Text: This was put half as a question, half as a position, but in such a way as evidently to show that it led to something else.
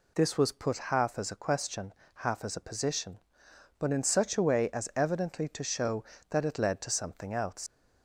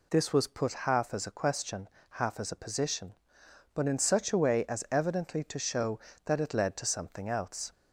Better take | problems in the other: second | leaves "else" unfinished; at 7.6 s; 90 ms

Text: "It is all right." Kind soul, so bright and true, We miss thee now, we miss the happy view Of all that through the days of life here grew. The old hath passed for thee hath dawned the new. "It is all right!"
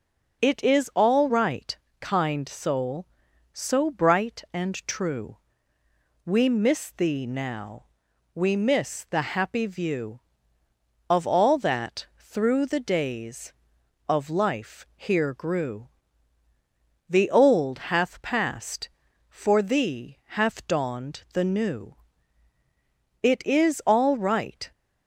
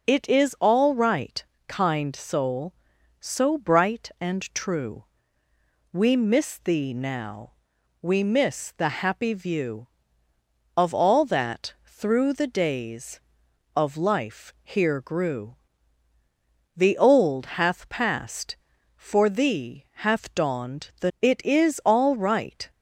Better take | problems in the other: first | skips "new"; at 21.1 s

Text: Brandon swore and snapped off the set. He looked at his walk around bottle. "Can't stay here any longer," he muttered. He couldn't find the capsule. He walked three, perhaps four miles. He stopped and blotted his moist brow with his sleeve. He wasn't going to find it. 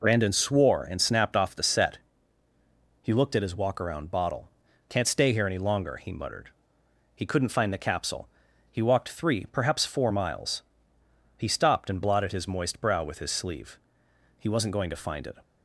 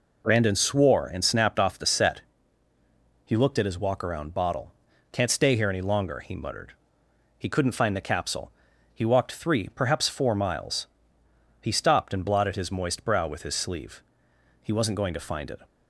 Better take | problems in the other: neither | none

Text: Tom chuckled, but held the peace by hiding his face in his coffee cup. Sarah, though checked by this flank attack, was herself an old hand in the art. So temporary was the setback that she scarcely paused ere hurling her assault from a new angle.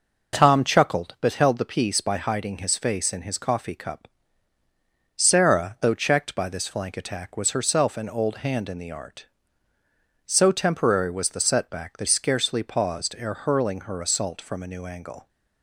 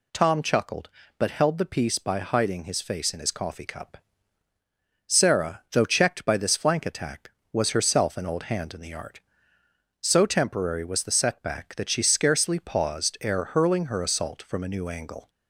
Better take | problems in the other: second | skips "she"; at 12.0 s

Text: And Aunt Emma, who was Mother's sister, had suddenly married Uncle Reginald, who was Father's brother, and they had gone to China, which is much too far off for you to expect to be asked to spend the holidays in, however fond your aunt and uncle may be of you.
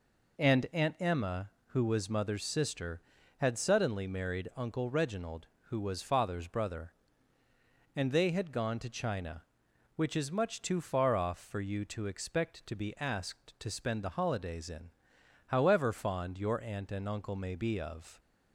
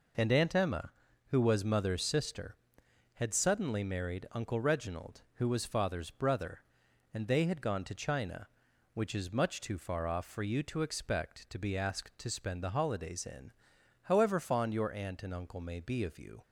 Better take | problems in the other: second | stops before "you"; at 18.1 s

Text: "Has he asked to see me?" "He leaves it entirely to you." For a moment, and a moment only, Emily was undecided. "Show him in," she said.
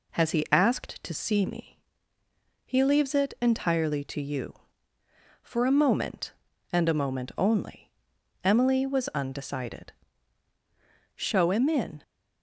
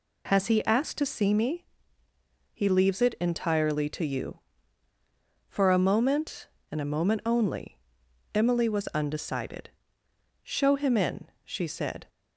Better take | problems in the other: second | stops before "she said"; at 12.0 s

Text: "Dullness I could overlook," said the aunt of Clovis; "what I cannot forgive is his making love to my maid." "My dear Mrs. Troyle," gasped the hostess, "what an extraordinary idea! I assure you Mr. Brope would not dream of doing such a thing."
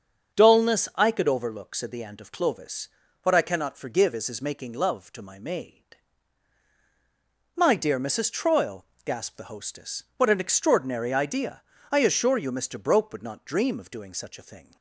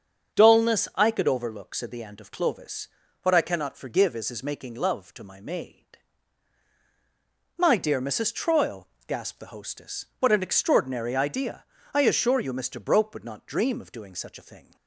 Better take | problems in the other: neither | starts louder than the rest; strong; the same in both

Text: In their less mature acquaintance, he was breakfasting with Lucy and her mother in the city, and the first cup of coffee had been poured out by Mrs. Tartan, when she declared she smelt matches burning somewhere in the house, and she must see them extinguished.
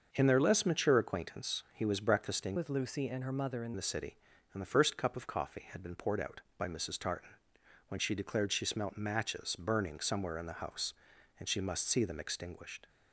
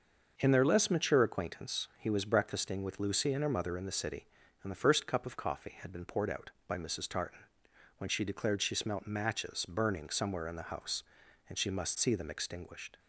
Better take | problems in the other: second | starts louder than the rest; until 1.1 s; 6.5 dB; also in the second // changes voice from "with" to "in"; from 2.5 to 3.7 s; 1.2 s long

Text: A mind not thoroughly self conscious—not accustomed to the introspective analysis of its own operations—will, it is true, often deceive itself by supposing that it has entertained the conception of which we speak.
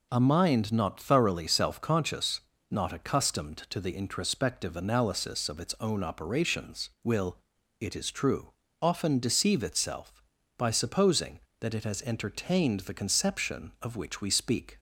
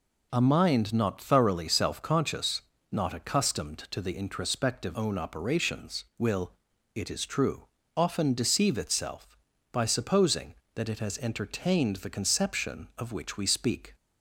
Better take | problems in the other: first | skips "analysis of its"; at 4.9 s

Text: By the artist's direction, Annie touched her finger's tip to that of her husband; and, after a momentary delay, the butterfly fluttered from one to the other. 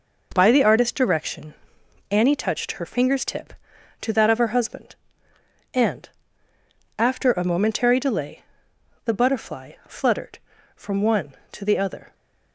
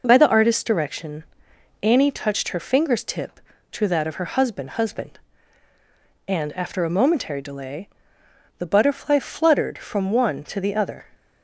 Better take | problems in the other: first | says "husband" twice; at 4.7 s

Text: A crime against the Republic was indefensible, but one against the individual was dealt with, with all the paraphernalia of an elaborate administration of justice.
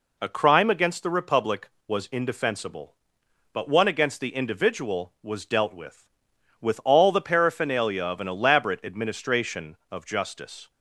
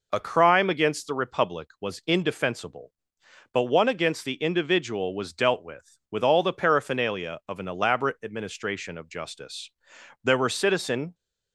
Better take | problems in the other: first | goes on to say "There were citizen"; noticeable; from 10.2 s on; 0.90 s long

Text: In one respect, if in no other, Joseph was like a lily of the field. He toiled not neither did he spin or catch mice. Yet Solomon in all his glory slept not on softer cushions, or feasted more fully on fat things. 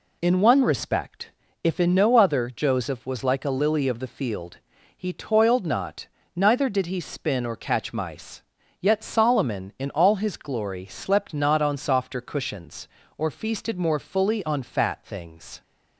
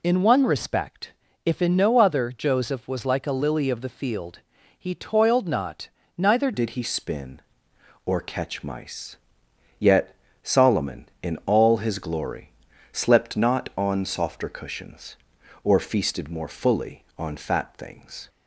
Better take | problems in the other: first | pauses between "not" and "neither"; slight; at 5.8 s; 0.28 s long; slight in the first // changes voice at "did"; from 6.5 s on; 11.7 s long // pauses between "Yet" and "Solomon"; slight; at 10.1 s; 0.28 s long // pauses between "glory" and "slept"; at 12.5 s; 0.42 s long

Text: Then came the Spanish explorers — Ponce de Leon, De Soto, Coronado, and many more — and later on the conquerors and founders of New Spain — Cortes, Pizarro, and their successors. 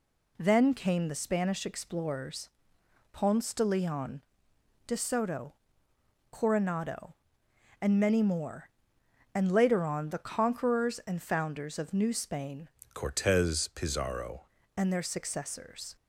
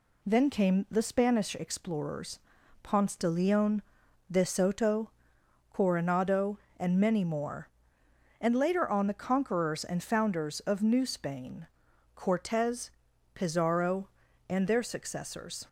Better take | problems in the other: second | changes voice from "Cortes" to "Pizarro"; from 12.9 to 14.4 s; 1.5 s long

